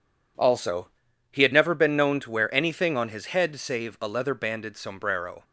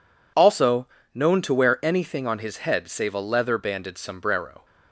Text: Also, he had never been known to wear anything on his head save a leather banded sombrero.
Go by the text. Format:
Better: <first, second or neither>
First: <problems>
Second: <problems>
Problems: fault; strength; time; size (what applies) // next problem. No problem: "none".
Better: first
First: none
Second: skips "he had never been"; at 0.9 s